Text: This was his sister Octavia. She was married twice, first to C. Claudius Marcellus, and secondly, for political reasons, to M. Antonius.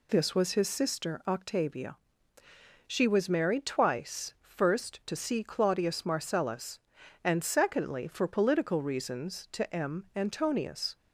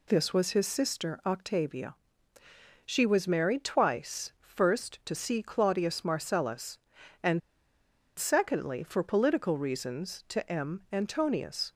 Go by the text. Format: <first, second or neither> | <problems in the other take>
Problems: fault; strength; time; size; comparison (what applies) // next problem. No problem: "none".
first | pauses between "and" and "secondly"; noticeable; at 7.4 s; 0.79 s long